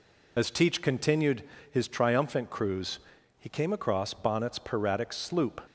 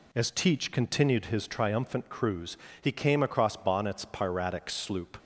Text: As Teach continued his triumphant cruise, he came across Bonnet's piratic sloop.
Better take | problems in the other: second | loses the start of "As"; at 0.3 s; 40 ms // pauses between "continued" and "his"; slight; at 1.4 s; 0.28 s long

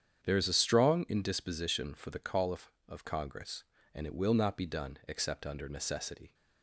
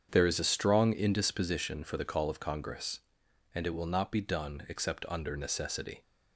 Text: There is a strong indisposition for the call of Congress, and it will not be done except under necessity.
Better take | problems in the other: second | starts louder than the rest; strong; until 1.2 s; 8.5 dB; strong in the second // says "of" twice; at 2.8 s

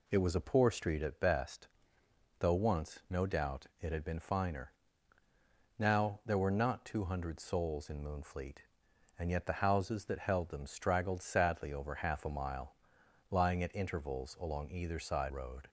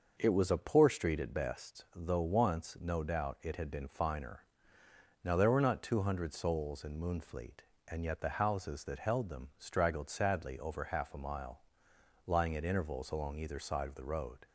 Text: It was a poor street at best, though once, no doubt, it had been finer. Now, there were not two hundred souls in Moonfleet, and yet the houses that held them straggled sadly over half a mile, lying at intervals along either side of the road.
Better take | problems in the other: second | skips "of the"; at 15.2 s

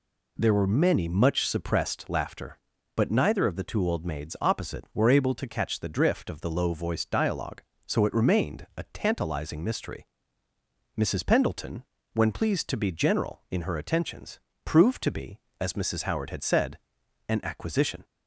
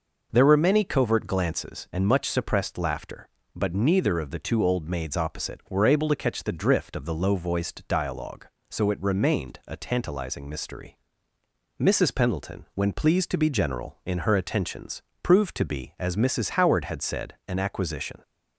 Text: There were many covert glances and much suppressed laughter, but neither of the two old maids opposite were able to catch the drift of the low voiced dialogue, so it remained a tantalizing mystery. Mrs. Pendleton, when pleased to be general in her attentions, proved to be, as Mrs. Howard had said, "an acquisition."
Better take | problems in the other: second | skips "covert glances and"; at 1.0 s

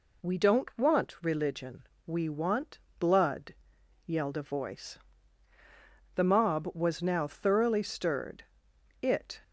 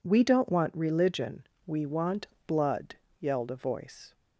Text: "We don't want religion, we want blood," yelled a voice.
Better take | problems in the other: second | pauses between "want" and "blood"; slight; at 2.7 s; 0.20 s long; slight in the second // goes on to say "The mob was now thoroughly stirred it"; strong; from 6.1 s on; 3.2 s long

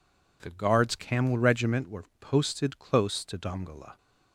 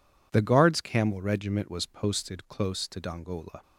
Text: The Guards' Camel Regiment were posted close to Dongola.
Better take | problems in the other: first | says "was" for "were"; at 1.7 s

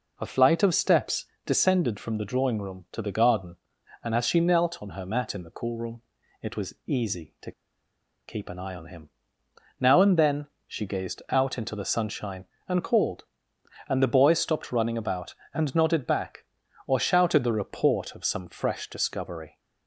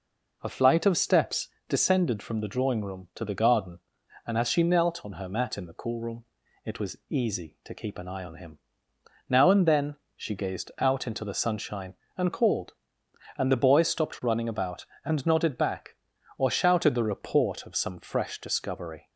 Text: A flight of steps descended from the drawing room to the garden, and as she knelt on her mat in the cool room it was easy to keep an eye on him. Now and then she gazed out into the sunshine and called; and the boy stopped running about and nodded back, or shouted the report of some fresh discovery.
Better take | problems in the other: second | pauses between "steps" and "descended"; slight; at 1.2 s; 0.18 s long; slight in the second // pauses between "room" and "it"; at 6.0 s; 0.40 s long; also in the second // pauses between "to" and "keep"; noticeable; at 7.5 s; 0.76 s long // pauses between "then" and "she"; slight; at 10.4 s; 0.20 s long; slight in the second

